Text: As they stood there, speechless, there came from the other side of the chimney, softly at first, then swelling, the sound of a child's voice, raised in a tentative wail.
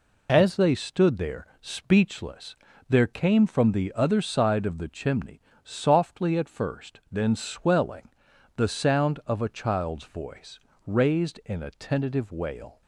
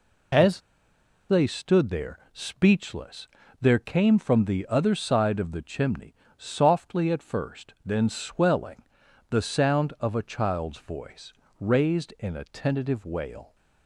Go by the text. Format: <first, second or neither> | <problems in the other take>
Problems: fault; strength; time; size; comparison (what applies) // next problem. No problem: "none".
first | pauses between "As" and "they"; noticeable; at 0.6 s; 0.67 s long